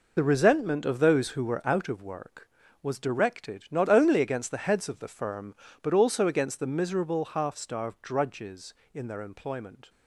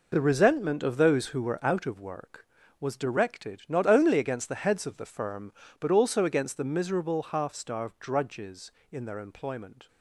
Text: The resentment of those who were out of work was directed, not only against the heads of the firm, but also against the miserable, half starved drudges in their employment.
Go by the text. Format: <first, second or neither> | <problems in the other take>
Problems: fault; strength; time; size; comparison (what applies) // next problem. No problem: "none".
second | loses the start of "The"; at 0.1 s; 25 ms